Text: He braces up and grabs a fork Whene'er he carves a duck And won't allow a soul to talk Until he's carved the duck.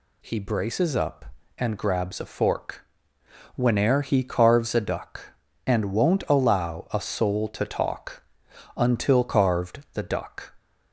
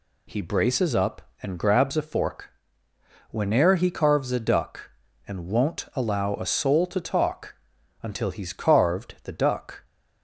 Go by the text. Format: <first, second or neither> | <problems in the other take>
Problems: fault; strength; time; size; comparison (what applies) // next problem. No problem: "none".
second | pauses between "fork" and "Whene'er"; noticeable; at 2.8 s; 0.72 s long; noticeable in the second // pauses between "talk" and "Until"; noticeable; at 8.2 s; 0.54 s long; noticeable in the second // skips "he's"; at 9.2 s